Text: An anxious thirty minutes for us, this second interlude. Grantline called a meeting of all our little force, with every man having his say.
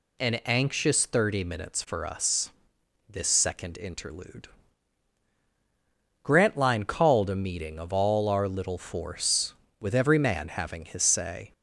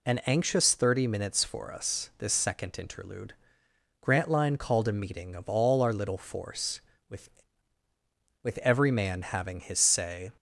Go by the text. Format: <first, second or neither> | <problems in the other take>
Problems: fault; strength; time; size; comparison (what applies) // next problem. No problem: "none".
first | says "with" twice; at 8.4 s